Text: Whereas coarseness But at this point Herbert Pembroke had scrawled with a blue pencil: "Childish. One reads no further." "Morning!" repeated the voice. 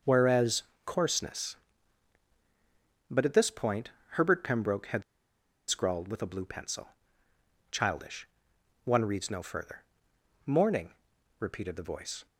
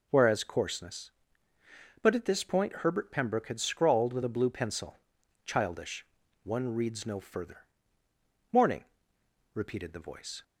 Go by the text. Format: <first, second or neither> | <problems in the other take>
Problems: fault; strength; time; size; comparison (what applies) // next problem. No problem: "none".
second | pauses between "Whereas" and "coarseness"; slight; at 0.6 s; 0.22 s long // pauses between "point" and "Herbert"; slight; at 3.9 s; 0.22 s long // pauses between "had" and "scrawled"; noticeable; at 5.0 s; 0.66 s long